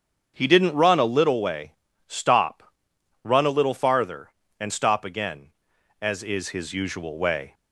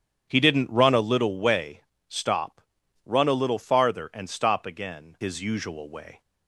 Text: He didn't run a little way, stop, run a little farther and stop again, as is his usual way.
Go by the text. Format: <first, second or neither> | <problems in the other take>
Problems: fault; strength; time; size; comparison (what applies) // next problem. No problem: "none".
first | starts louder than the rest; strong; until 1.3 s; 9 dB; strong in the first // skips "as is"; at 5.1 s